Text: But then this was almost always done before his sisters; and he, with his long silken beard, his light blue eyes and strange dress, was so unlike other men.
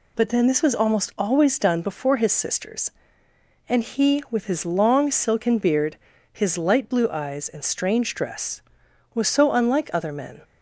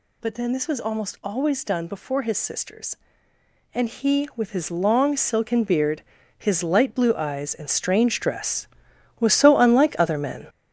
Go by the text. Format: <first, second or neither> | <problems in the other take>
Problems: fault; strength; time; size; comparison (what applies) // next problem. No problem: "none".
first | gets louder; strong; throughout; 8 dB